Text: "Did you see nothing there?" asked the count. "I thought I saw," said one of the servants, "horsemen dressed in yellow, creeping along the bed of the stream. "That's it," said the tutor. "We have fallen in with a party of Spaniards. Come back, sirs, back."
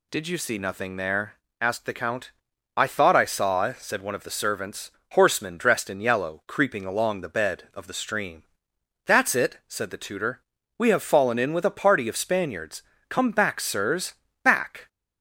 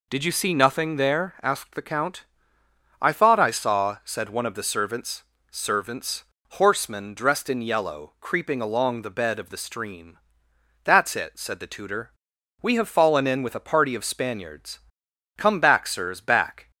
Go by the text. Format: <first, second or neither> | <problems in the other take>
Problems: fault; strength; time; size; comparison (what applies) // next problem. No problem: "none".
first | says "servants" twice; at 5.5 s